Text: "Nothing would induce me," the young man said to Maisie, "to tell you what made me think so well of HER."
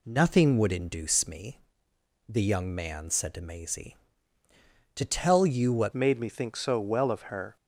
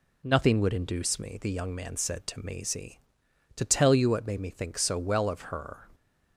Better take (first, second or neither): second